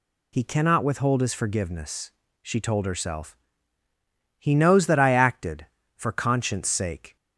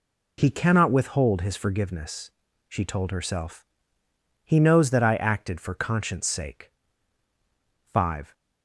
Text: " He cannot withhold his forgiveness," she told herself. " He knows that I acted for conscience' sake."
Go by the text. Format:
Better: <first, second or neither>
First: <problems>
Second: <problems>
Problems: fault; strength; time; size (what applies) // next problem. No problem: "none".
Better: first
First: none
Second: goes on to say "Five"; slight; from 7.9 s on; 0.42 s long